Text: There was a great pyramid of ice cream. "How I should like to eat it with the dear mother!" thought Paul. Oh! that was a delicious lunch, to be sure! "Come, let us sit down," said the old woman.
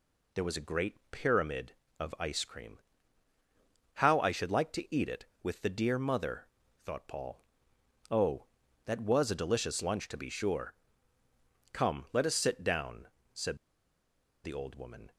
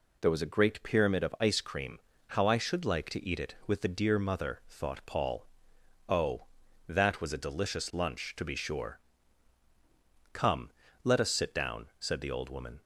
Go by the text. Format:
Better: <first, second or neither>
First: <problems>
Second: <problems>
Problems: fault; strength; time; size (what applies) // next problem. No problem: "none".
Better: second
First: pauses between "said" and "the"; noticeable; at 13.5 s; 0.87 s long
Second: none